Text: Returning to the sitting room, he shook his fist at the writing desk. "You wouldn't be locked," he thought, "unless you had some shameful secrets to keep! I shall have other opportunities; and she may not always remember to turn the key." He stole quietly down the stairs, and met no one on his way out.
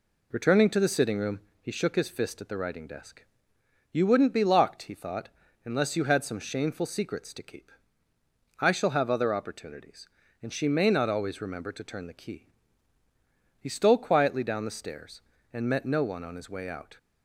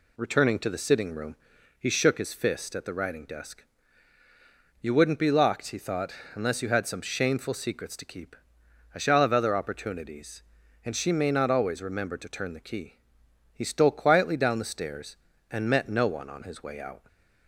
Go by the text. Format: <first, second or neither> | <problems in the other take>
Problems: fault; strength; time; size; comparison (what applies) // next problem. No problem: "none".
neither | none